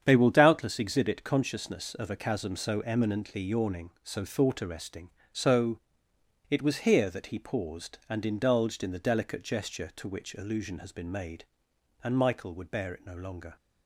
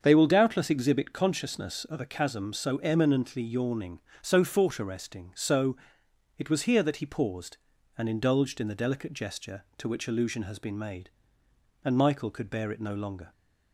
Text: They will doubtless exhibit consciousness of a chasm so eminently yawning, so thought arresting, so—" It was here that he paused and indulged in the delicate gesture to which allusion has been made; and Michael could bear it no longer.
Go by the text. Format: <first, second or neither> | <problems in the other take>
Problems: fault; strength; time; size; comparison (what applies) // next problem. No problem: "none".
second | starts louder than the rest; strong; until 1.0 s; 8 dB; also in the second // says "would" for "could"; at 12.5 s